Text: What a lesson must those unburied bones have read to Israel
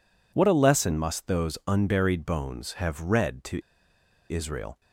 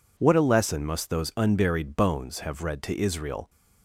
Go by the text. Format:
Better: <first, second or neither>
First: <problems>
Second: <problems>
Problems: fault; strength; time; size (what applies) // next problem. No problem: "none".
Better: second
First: pauses between "to" and "Israel"; noticeable; at 3.6 s; 0.67 s long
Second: none